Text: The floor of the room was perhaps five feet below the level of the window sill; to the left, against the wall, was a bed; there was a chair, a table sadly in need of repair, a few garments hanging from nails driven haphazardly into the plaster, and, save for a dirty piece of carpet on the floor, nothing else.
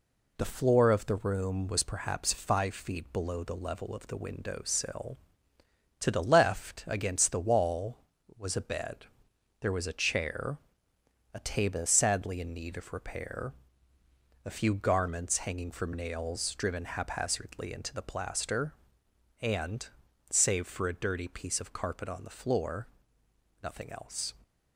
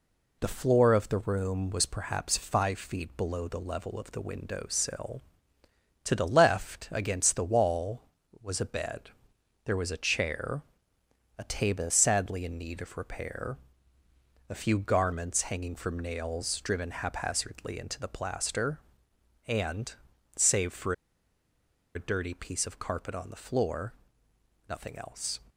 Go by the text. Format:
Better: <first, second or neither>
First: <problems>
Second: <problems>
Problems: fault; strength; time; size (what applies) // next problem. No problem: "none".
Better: first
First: none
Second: pauses between "for" and "a"; at 20.9 s; 1.0 s long